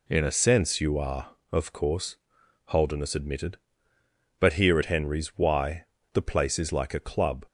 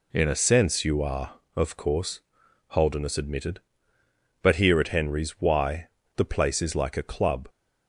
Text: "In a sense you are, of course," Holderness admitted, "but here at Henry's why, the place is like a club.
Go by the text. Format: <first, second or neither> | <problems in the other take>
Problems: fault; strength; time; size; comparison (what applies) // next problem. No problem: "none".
neither | none